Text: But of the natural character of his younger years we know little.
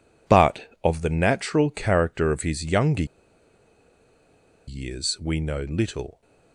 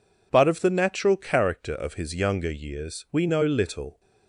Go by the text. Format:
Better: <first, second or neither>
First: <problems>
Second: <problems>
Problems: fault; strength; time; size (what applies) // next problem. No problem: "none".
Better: second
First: pauses between "younger" and "years"; strong; at 3.0 s; 1.6 s long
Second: none